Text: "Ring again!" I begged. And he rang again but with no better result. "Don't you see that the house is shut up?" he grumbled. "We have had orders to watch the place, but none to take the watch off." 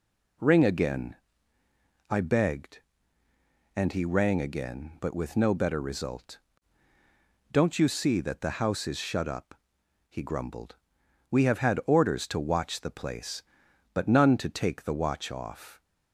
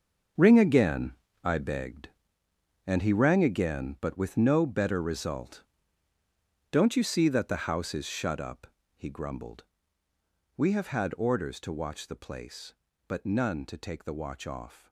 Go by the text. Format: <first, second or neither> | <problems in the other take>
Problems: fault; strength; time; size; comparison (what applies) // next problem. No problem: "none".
first | gets quieter; strong; throughout; 12 dB